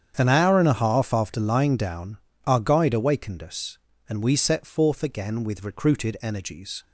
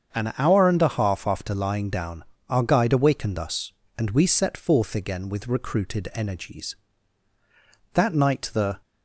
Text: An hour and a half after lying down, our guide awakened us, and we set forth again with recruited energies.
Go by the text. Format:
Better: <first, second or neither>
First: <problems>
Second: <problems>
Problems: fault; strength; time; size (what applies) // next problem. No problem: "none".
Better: first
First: starts louder than the rest; strong; until 1.1 s; 8.5 dB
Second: starts louder than the rest; until 1.1 s; 7 dB // goes on to say "That night the"; noticeable; from 7.9 s on; 0.88 s long